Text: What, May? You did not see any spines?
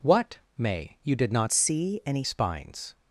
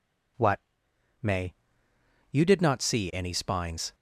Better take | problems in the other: second | changes voice from "see" to "any"; from 1.5 to 2.2 s; 0.7 s long

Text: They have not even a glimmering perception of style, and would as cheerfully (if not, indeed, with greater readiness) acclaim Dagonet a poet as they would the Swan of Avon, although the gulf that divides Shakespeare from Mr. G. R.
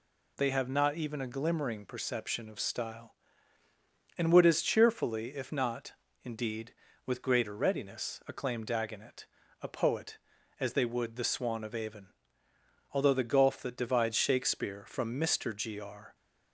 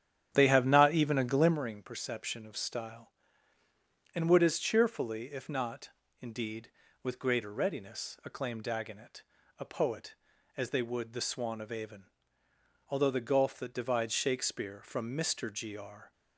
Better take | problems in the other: first | starts louder than the rest; strong; until 1.6 s; 9.5 dB // pauses between "Dagonet" and "a"; slight; at 9.2 s; 0.34 s long; slight in the first

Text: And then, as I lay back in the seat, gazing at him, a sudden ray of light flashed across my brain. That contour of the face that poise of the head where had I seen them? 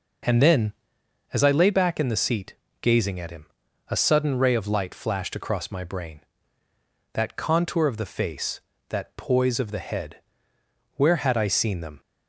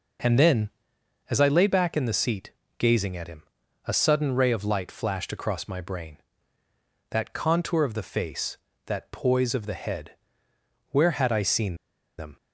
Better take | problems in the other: first | pauses between "head" and "where"; noticeable; at 10.1 s; 0.76 s long; noticeable in the first // pauses between "seen" and "them"; at 11.7 s; 0.41 s long

